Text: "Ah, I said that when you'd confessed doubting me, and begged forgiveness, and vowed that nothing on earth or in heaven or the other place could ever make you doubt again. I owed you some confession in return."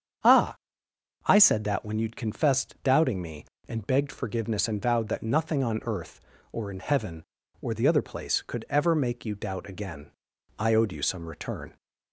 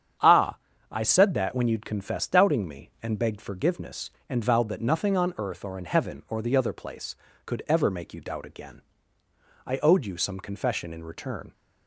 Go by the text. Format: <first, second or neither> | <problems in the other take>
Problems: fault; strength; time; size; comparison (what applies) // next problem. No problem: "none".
second | starts louder than the rest; strong; until 1.9 s; 8 dB; strong in the second // skips "confession in"; at 11.2 s